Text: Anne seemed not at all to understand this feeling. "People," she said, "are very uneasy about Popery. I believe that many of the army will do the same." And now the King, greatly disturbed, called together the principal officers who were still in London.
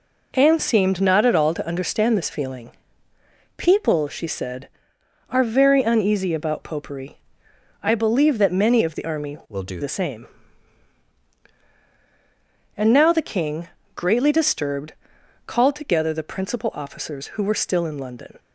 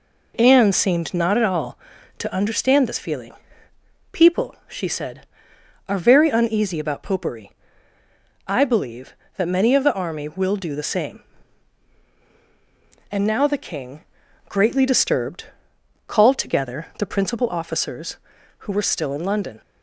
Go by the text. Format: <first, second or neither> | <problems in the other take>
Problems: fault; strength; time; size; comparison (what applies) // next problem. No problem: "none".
second | changes voice from "will" to "do"; from 9.4 to 9.8 s; 0.4 s long